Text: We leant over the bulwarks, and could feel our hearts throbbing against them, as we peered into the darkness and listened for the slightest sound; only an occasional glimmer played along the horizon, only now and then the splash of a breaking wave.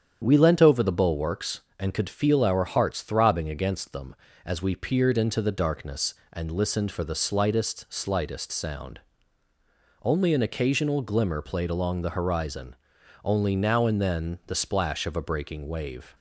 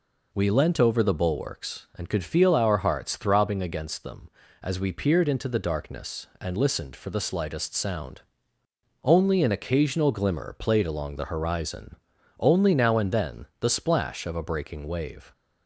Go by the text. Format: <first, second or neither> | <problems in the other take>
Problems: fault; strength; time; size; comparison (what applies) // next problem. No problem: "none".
second | starts louder than the rest; strong; until 1.2 s; 8.5 dB // says "slightest" twice; at 7.9 s